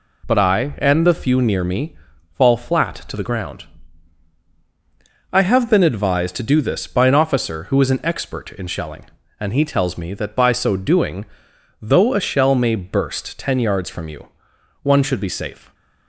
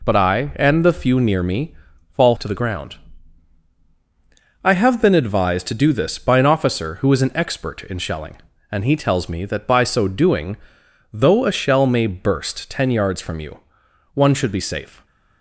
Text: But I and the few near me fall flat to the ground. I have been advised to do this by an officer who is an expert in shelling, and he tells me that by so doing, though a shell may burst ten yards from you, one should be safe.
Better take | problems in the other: first | pauses between "me" and "fall"; slight; at 1.7 s; 0.36 s long; slight in the first // skips "flat"; at 2.3 s

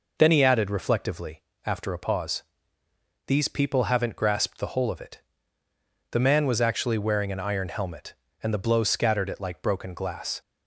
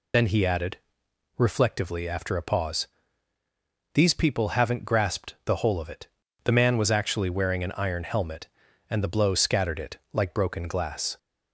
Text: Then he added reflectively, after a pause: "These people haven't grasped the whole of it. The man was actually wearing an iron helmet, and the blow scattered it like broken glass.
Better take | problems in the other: first | loses the start of "Then"; at 0.1 s; 30 ms // pauses between "added" and "reflectively"; noticeable; at 0.7 s; 0.60 s long // pauses between "it" and "like"; slight; at 9.9 s; 0.16 s long

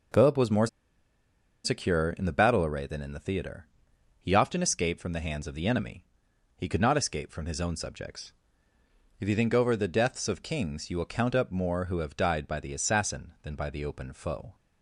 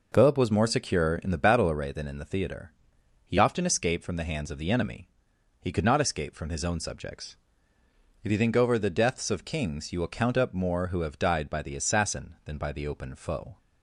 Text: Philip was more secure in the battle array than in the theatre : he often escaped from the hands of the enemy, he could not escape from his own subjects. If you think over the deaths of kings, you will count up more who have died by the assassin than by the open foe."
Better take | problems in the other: second | pauses between "more" and "secure"; noticeable; at 0.6 s; 0.97 s long

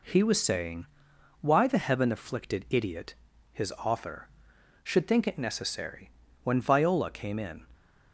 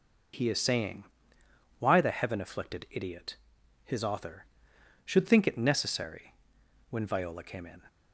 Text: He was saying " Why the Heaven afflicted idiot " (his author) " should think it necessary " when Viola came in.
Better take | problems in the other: first | says "is" for "was"; at 0.4 s

